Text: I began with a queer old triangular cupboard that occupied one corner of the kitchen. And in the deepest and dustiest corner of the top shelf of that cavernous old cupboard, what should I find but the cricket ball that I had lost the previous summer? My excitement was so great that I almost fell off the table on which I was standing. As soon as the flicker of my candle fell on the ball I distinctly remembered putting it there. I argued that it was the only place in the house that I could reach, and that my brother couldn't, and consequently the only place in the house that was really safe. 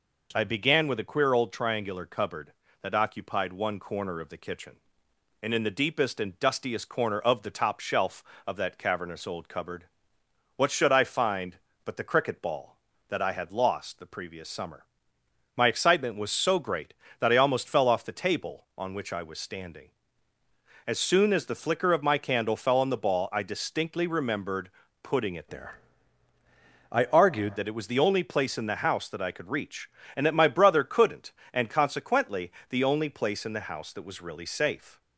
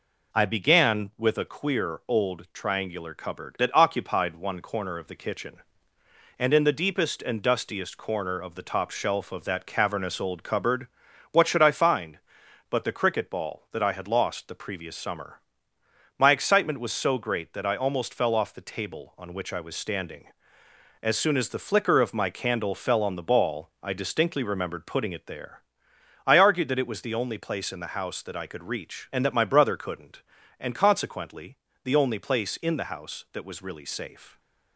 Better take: second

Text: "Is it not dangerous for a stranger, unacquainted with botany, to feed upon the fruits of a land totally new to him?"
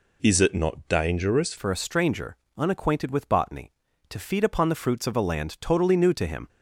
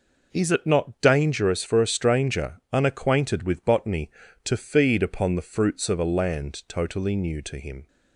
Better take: second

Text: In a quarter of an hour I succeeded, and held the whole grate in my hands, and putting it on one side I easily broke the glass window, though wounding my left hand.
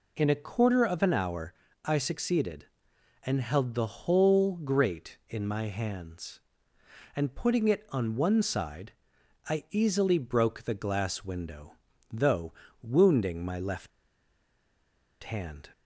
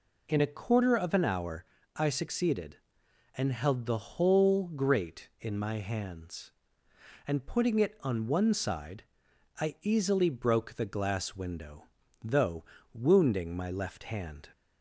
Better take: second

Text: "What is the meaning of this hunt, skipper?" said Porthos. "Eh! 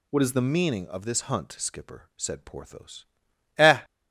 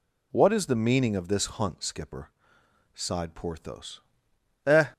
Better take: first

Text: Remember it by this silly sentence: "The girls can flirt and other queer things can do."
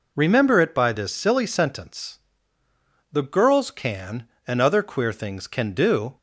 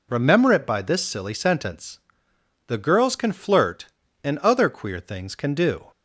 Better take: second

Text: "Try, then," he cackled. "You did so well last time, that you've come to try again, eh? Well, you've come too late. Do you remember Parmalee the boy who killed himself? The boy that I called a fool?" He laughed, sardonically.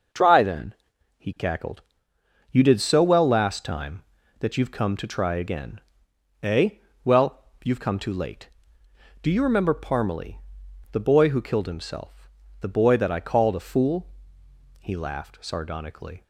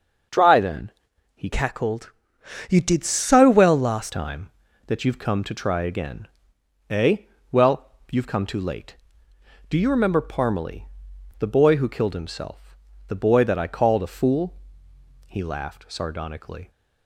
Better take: first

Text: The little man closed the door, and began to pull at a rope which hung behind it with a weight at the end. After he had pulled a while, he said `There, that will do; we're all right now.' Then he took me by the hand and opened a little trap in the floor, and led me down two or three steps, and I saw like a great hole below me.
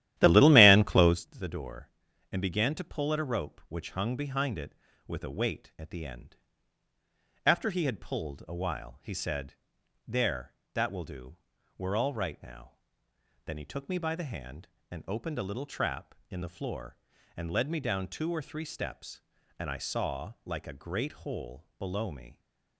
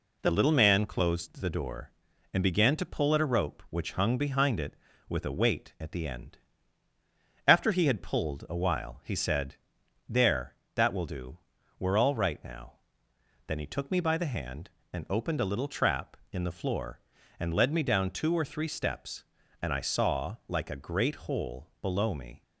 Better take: second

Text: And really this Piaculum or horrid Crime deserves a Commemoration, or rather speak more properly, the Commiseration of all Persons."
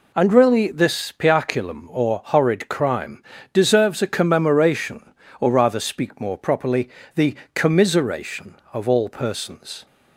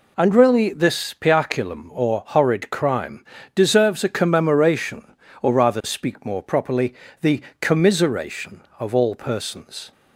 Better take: neither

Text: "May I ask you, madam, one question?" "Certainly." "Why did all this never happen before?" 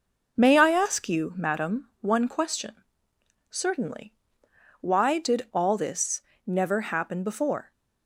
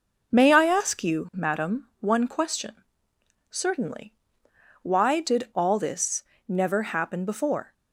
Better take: neither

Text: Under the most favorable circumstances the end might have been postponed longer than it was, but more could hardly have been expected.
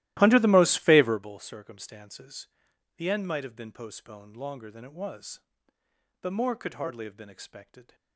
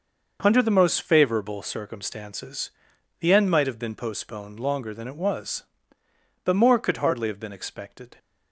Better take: second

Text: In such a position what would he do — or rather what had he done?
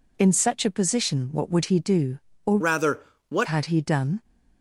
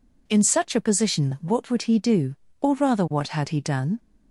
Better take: second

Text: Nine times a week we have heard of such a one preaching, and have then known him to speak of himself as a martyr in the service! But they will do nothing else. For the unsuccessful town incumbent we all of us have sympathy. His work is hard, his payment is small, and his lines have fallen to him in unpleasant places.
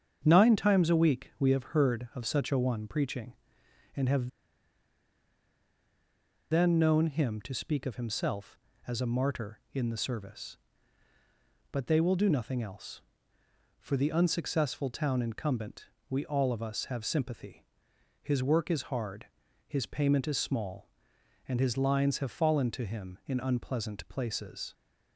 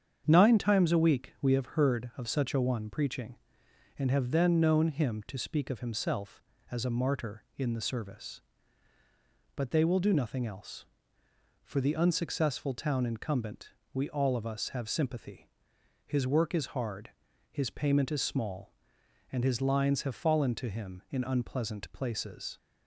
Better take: second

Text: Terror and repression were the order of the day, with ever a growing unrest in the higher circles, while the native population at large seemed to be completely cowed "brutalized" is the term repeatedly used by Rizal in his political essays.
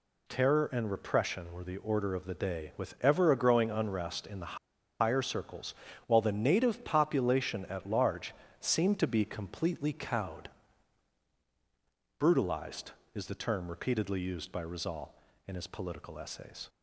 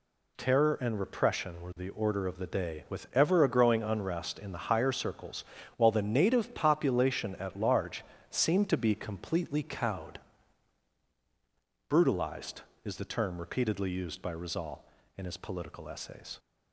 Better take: second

